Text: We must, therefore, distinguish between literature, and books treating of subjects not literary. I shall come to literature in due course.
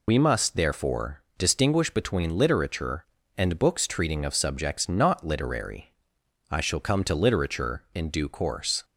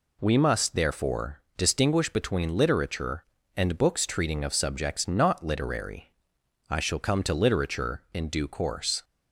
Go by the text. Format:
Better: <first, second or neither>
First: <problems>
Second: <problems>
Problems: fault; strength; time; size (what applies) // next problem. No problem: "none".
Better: second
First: loses the start of "We"; at 0.0 s; 75 ms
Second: none